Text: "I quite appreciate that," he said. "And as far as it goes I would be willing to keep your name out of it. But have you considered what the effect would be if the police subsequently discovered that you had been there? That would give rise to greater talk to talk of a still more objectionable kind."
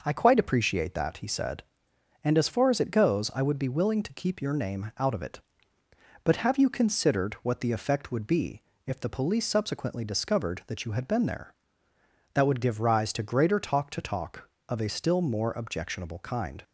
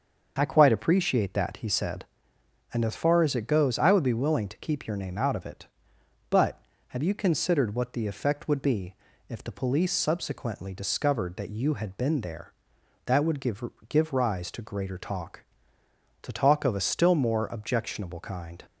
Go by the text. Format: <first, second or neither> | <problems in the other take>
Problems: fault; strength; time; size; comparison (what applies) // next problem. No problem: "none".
first | starts louder than the rest; until 1.3 s; 6.5 dB // pauses between "be" and "if"; slight; at 8.9 s; 0.36 s long; slight in the first // says "give" twice; at 13.8 s